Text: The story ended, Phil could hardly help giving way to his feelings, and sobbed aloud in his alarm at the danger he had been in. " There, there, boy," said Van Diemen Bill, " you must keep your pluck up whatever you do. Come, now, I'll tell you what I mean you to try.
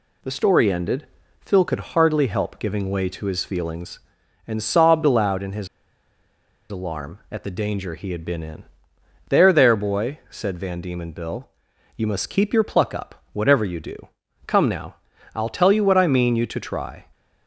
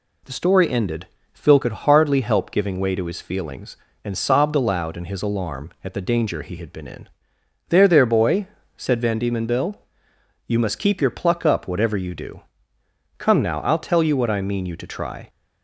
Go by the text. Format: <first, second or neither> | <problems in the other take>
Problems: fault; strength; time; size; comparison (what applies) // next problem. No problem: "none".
second | pauses between "his" and "alarm"; at 5.6 s; 1.0 s long